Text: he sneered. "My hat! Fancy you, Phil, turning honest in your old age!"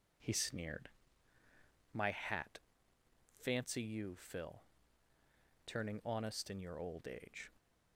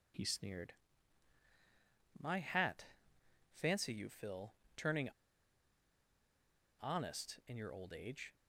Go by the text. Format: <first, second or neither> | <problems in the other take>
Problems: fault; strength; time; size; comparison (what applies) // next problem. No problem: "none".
first | pauses between "turning" and "honest"; strong; at 5.0 s; 1.6 s long